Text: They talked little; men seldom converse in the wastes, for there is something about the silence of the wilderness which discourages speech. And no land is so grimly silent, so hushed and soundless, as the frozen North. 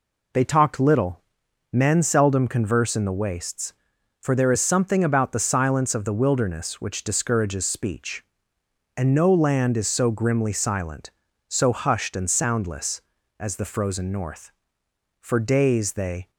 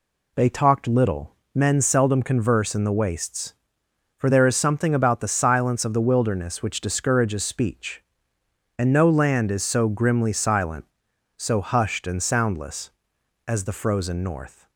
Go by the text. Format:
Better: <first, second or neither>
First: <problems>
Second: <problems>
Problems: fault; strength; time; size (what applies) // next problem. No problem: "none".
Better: second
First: goes on to say "For days they"; noticeable; from 15.1 s on; 1.1 s long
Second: none